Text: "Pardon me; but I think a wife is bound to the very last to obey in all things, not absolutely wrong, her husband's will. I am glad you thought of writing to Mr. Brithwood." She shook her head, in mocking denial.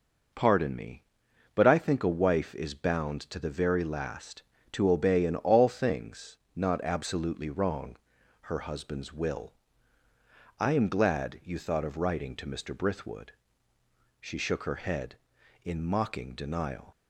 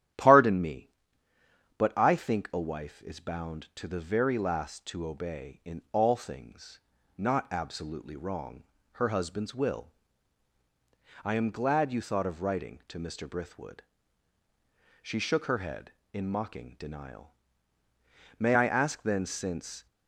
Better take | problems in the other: first | starts louder than the rest; strong; until 2.0 s; 11 dB // goes on to say "May I ask then since"; from 18.3 s on; 1.4 s long

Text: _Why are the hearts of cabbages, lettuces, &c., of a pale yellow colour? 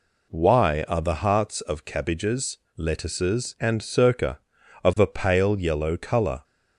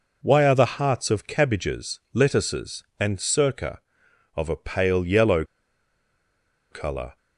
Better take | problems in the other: first | pauses between "yellow" and "colour"; strong; at 5.4 s; 1.2 s long

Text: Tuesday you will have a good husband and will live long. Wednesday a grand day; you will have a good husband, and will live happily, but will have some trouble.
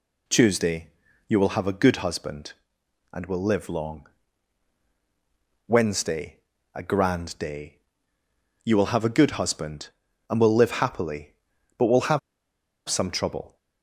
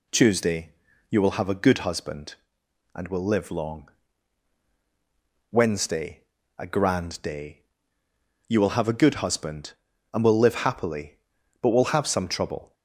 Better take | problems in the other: second | pauses between "Tuesday" and "you"; at 0.8 s; 0.40 s long; also in the second // pauses between "Wednesday" and "a"; at 6.3 s; 0.38 s long; also in the second // pauses between "have" and "some"; noticeable; at 12.1 s; 0.68 s long

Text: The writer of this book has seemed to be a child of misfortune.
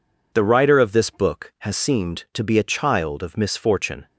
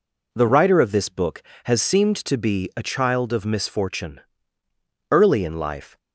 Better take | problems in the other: first | goes on to say "Early in life"; noticeable; from 5.0 s on; 0.88 s long

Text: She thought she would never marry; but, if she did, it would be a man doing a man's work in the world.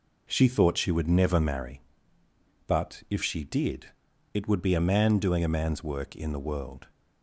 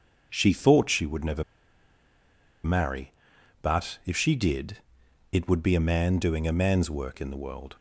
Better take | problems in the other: first | starts louder than the rest; until 1.3 s; 6.5 dB // pauses between "never" and "marry"; at 1.4 s; 1.2 s long

